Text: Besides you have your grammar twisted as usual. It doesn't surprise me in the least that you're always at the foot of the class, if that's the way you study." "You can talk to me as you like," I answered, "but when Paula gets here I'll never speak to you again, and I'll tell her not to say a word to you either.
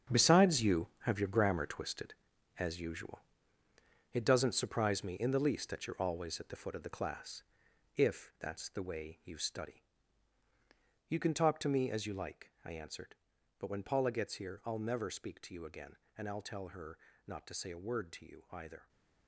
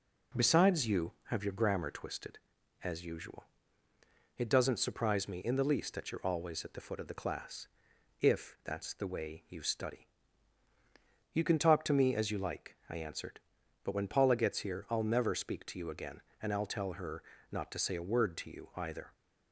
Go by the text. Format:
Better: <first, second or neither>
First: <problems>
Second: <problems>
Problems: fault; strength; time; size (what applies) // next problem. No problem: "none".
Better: second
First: gets quieter; strong; throughout; 11.5 dB // pauses between "her" and "not"; slight; at 16.9 s; 0.28 s long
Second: pauses between "her" and "not"; slight; at 17.2 s; 0.28 s long